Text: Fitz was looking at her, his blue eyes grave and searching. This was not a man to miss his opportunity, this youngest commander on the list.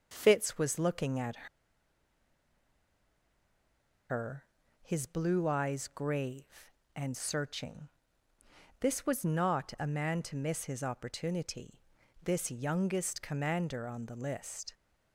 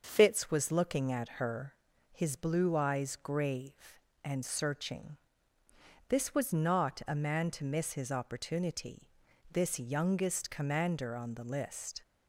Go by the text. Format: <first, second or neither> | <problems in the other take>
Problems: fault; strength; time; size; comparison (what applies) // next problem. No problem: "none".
second | starts louder than the rest; until 1.1 s; 6.5 dB; also in the second // pauses between "at" and "her"; strong; at 1.4 s; 2.6 s long